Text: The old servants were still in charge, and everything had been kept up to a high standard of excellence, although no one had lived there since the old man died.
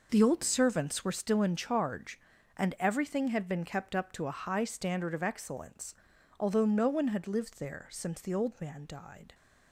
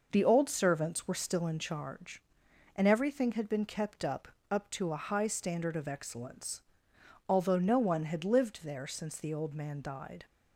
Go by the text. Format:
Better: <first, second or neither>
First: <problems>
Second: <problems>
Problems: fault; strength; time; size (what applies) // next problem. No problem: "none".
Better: first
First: none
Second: says "up" twice; at 4.5 s